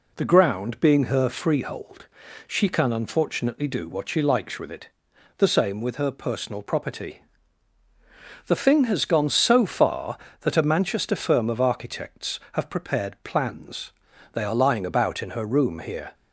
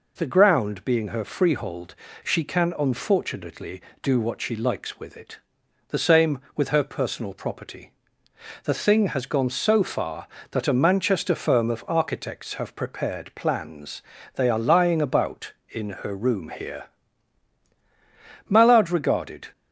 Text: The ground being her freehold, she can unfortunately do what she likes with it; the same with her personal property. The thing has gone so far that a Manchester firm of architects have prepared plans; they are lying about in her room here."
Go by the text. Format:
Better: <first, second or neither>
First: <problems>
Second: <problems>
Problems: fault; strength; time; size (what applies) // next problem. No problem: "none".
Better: first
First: none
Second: goes on to say "Mallard regarded"; noticeable; from 18.4 s on; 1.0 s long